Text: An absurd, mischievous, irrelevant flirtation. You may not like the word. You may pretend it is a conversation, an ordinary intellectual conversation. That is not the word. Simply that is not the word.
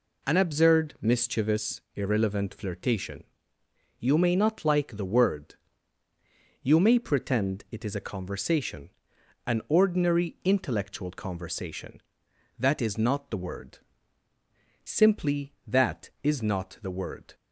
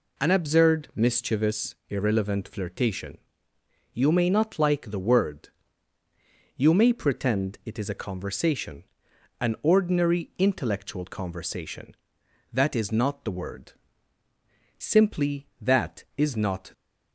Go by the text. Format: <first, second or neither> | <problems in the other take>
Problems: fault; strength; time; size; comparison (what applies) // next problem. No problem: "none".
first | stops before "the word"; at 16.7 s